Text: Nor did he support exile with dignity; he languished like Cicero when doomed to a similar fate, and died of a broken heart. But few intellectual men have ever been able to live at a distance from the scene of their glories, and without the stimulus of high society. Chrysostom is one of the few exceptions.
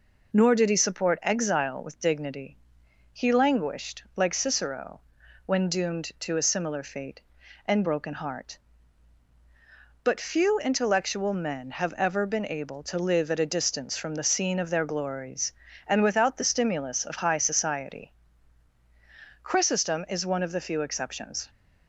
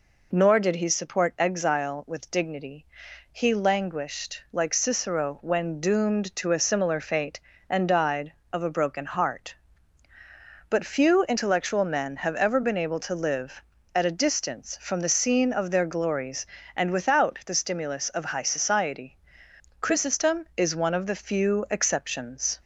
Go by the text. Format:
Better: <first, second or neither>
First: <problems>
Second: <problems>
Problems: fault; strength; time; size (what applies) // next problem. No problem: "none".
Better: second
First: pauses between "Cicero" and "when"; at 5.0 s; 0.44 s long // skips "died of a"; at 7.8 s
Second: none